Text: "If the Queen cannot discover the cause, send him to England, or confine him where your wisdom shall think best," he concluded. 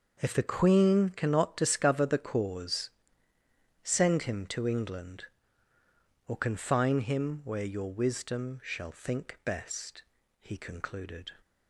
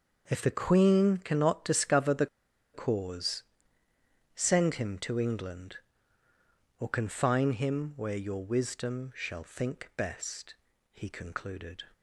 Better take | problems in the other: first | pauses between "the" and "cause"; noticeable; at 2.2 s; 0.47 s long

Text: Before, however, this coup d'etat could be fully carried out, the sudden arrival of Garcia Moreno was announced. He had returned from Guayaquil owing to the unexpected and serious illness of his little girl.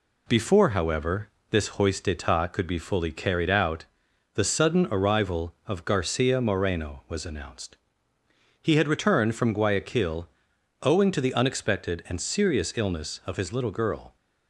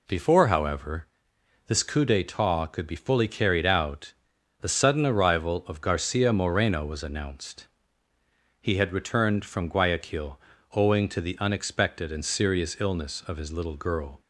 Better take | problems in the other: second | says "hoist" for "coup"; at 1.7 s // pauses between "Guayaquil" and "owing"; noticeable; at 10.2 s; 0.54 s long; slight in the second

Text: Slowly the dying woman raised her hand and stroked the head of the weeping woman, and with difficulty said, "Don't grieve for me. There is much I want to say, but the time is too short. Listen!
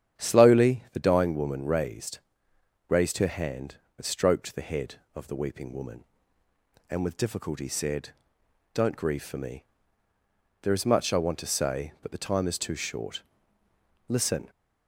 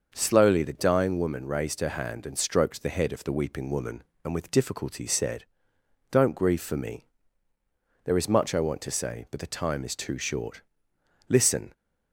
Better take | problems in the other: second | starts louder than the rest; strong; until 1.2 s; 9 dB; also in the second // says "raised" twice; at 2.8 s

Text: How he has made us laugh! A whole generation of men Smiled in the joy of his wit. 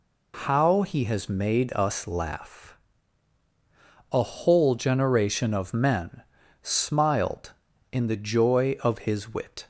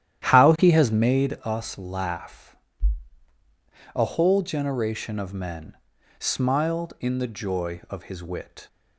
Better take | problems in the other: first | starts louder than the rest; strong; until 1.4 s; 11 dB // pauses between "men" and "Smiled"; at 5.7 s; 0.40 s long; also in the first

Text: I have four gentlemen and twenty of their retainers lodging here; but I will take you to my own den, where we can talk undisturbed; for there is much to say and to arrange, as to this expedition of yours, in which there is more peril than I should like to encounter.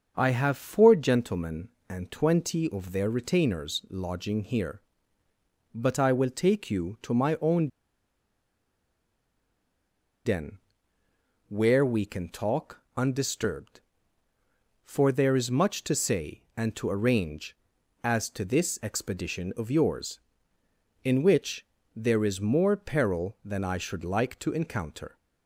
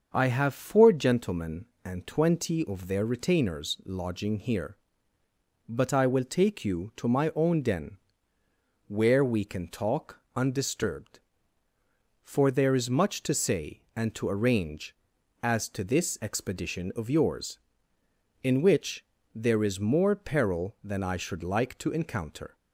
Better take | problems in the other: second | starts louder than the rest; until 1.1 s; 6.5 dB; also in the second // pauses between "own" and "den"; strong; at 7.6 s; 2.5 s long // pauses between "talk" and "undisturbed"; slight; at 12.7 s; 0.18 s long; slight in the second // pauses between "which" and "there"; slight; at 21.6 s; 0.30 s long; slight in the second

